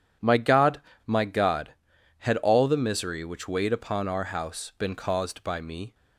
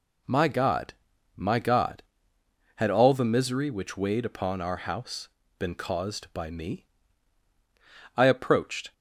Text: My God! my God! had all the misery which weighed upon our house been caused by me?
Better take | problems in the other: first | pauses between "house" and "been"; slight; at 5.2 s; 0.30 s long // goes on to say "I approached"; noticeable; from 8.1 s on; 0.76 s long

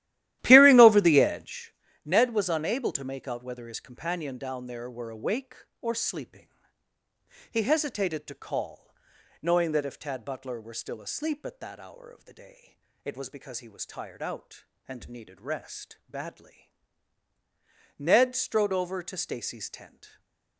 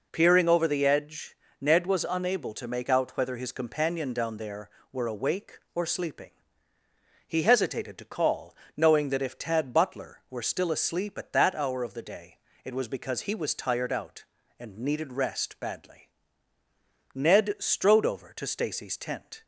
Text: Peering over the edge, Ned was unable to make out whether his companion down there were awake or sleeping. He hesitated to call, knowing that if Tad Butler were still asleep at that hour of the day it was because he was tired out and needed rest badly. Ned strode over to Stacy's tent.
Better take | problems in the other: second | starts louder than the rest; strong; until 1.7 s; 14 dB // pauses between "day" and "it"; slight; at 12.7 s; 0.30 s long; slight in the second // stays silent after the last word; slight; from 20.0 s on; 0.5 s long

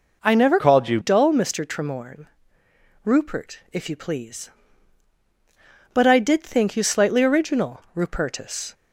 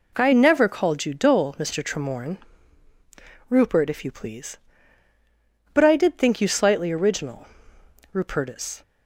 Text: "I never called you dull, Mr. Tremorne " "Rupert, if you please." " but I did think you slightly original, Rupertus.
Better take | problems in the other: second | changes voice from "called" to "you"; from 0.5 to 0.9 s; 0.4 s long

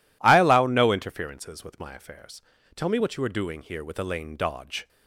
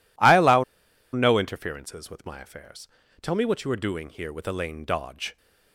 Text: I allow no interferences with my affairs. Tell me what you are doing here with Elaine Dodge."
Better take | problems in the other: first | pauses between "allow" and "no"; noticeable; at 0.6 s; 0.48 s long

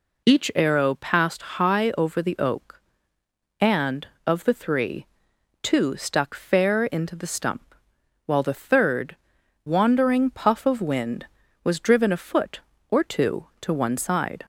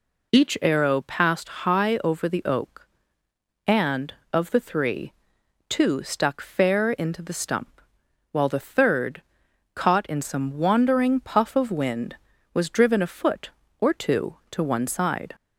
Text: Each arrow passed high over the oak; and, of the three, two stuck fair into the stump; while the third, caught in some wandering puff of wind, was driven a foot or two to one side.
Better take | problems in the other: second | pauses between "passed" and "high"; slight; at 1.4 s; 0.16 s long; slight in the second // skips "caught in some"; at 9.4 s

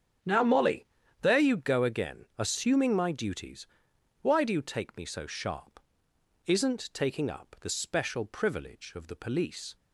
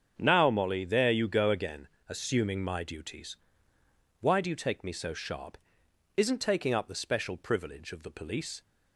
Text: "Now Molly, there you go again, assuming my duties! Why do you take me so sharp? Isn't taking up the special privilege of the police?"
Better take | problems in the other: neither | starts louder than the rest; strong; the same in both

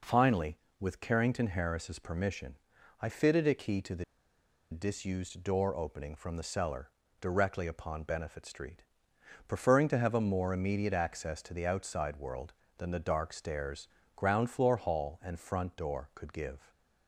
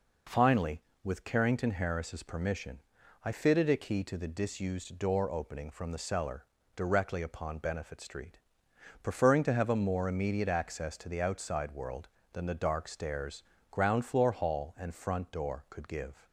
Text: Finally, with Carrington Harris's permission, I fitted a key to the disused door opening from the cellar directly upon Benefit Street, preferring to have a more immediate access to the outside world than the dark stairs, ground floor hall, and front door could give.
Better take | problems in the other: second | pauses between "the" and "disused"; noticeable; at 4.0 s; 0.67 s long // pauses between "cellar" and "directly"; slight; at 6.9 s; 0.28 s long; slight in the second

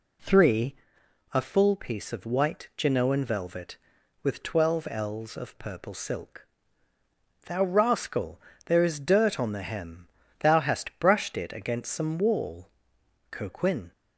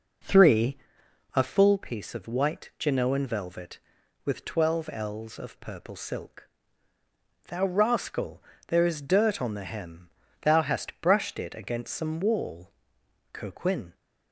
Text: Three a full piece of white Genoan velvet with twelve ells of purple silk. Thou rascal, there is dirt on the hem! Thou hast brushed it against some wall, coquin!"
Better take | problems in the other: first | starts louder than the rest; noticeable; until 1.9 s; 5.5 dB // pauses between "Three" and "a"; noticeable; at 0.7 s; 0.56 s long; noticeable in the first

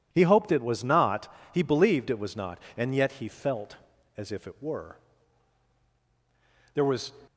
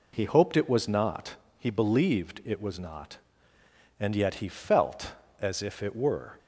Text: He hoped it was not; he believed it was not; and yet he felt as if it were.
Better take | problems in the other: second | goes on to say "There was"; slight; from 6.7 s on; 0.40 s long

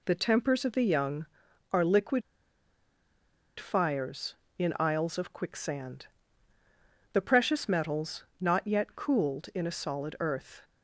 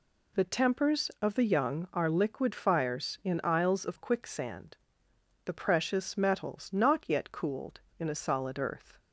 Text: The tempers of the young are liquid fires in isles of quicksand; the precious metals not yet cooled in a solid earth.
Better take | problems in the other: second | pauses between "liquid" and "fires"; strong; at 2.2 s; 1.3 s long // pauses between "metals" and "not"; slight; at 8.2 s; 0.16 s long

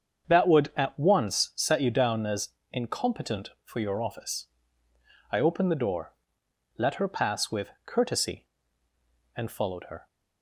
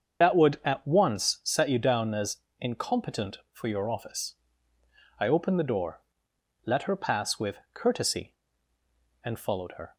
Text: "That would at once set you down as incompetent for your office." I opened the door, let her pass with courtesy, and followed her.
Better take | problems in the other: first | loses the start of "That"; at 0.2 s; 60 ms // starts louder than the rest; until 1.2 s; 7 dB; strong in the first // pauses between "as" and "incompetent"; slight; at 2.3 s; 0.22 s long; slight in the first

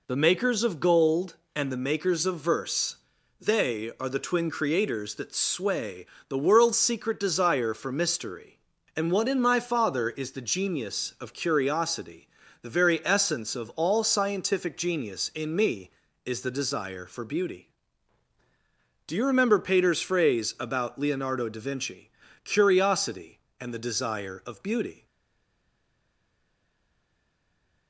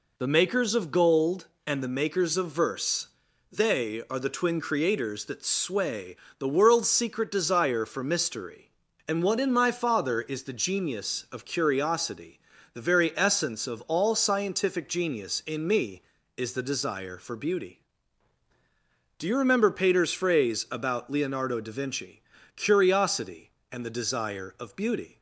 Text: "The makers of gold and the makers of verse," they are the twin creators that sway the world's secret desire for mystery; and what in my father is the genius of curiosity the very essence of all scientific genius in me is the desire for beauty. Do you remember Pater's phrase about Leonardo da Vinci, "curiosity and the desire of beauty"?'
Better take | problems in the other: second | pauses between "sway" and "the"; slight; at 6.0 s; 0.24 s long; slight in the second // pauses between "curiosity" and "the"; slight; at 12.2 s; 0.36 s long; slight in the second // stays silent after the last word; strong; from 25.0 s on; 2.8 s long

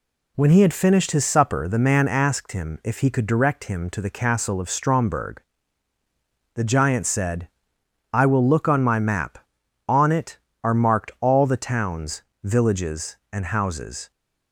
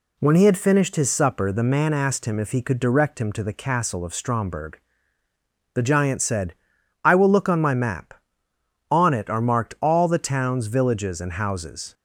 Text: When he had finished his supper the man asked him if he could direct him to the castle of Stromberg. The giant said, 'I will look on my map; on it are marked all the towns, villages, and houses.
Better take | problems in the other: neither | none

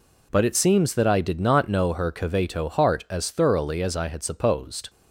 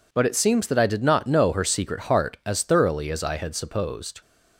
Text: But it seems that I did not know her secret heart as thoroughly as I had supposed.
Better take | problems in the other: second | says "caveto" for "secret"; at 2.1 s

